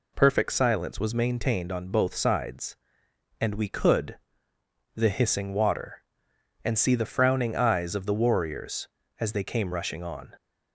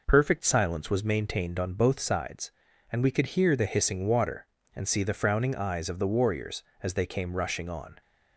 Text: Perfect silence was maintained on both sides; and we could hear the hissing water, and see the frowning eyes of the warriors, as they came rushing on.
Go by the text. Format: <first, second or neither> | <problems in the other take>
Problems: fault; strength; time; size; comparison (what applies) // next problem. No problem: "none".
second | skips "hear"; at 4.5 s